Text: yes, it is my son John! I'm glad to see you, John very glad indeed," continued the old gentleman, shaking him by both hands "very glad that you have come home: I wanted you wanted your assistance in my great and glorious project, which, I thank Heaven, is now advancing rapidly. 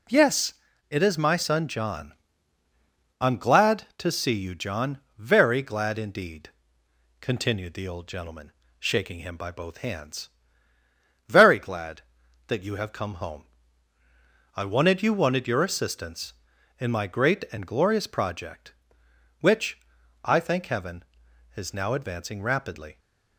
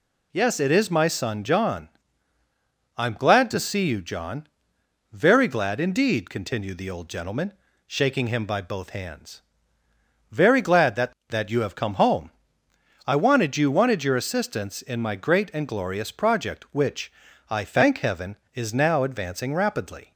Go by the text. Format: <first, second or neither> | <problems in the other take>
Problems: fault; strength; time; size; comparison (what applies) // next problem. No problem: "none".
first | pauses between "John" and "very"; noticeable; at 4.4 s; 0.64 s long; slight in the first // pauses between "hands" and "very"; noticeable; at 9.4 s; 0.90 s long; also in the first // says "that" twice; at 11.3 s